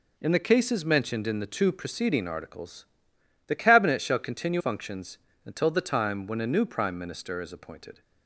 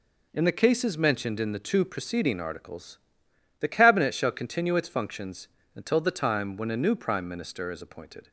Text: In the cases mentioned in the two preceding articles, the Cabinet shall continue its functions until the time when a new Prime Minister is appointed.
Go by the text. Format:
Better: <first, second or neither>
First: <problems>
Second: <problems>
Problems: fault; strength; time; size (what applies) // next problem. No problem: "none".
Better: second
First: skips "its"; at 4.6 s // pauses between "functions" and "until"; slight; at 5.1 s; 0.26 s long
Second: pauses between "functions" and "until"; slight; at 5.4 s; 0.26 s long